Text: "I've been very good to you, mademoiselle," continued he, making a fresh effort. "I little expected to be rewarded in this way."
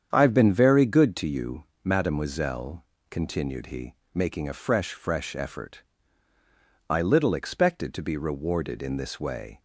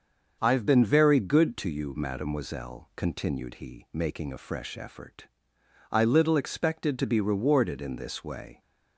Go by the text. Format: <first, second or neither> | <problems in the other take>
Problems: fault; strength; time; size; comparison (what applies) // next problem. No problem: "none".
second | starts louder than the rest; strong; until 1.1 s; 8 dB; also in the second // says "fresh" twice; at 4.9 s